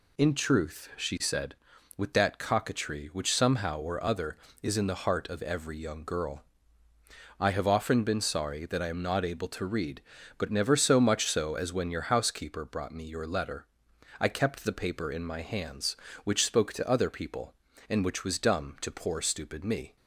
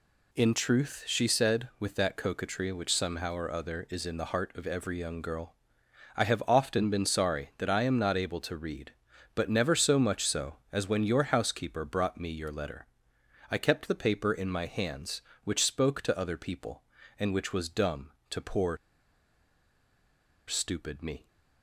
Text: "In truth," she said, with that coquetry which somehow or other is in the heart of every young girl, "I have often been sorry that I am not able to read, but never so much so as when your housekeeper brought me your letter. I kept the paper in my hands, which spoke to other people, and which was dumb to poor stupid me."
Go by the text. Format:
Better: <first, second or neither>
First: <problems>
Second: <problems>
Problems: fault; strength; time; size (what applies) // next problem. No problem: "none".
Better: first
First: none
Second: pauses between "poor" and "stupid"; strong; at 18.7 s; 1.7 s long